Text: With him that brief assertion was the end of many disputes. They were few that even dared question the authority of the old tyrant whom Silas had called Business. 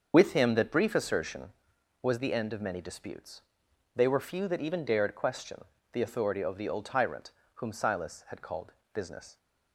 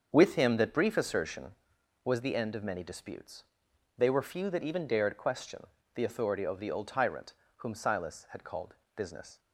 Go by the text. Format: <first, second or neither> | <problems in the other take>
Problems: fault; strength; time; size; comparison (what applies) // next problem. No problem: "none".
second | loses the start of "With"; at 0.1 s; 30 ms // starts louder than the rest; until 1.1 s; 6.5 dB; also in the second // pauses between "question" and "the"; slight; at 5.6 s; 0.28 s long; slight in the second // pauses between "tyrant" and "whom"; slight; at 7.2 s; 0.26 s long; slight in the second // pauses between "called" and "Business"; slight; at 8.7 s; 0.18 s long; slight in the second